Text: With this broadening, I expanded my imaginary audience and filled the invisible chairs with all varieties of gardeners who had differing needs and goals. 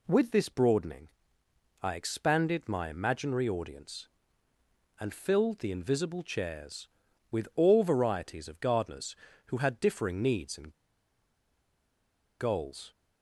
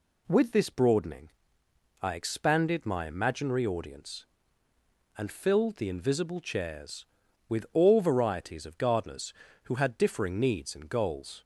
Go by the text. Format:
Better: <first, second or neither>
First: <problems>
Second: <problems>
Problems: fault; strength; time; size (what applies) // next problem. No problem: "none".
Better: second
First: pauses between "and" and "goals"; strong; at 10.7 s; 1.6 s long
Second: none